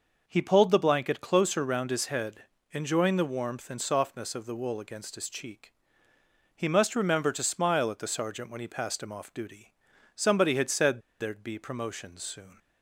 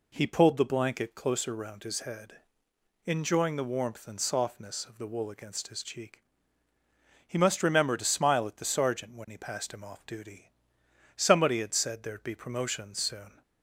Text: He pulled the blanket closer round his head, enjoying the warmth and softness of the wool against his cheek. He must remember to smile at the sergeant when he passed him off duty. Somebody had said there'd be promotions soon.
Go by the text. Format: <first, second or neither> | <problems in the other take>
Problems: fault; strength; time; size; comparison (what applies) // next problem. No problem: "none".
second | pauses between "said" and "there'd"; slight; at 11.0 s; 0.19 s long